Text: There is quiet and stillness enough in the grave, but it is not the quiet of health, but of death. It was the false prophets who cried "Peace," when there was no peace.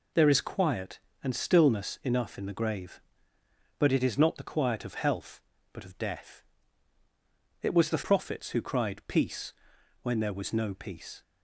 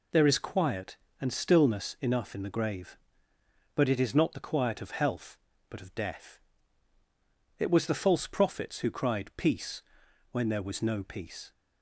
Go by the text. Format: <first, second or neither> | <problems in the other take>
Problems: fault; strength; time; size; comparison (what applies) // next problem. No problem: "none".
second | skips "false"; at 8.0 s